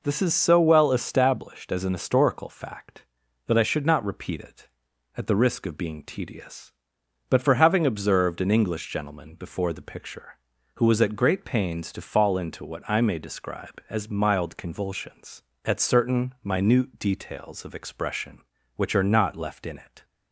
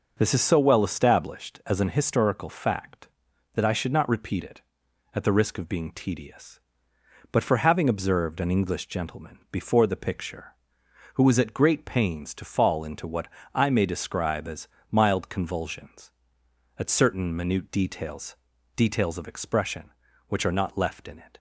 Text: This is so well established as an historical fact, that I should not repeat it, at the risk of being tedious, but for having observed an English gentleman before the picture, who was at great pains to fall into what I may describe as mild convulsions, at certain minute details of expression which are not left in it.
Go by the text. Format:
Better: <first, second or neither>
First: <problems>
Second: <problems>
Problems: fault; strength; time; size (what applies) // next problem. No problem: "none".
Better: first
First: none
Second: pauses between "what" and "I"; slight; at 13.2 s; 0.26 s long // pauses between "as" and "mild"; slight; at 14.6 s; 0.22 s long // says "details" twice; at 18.7 s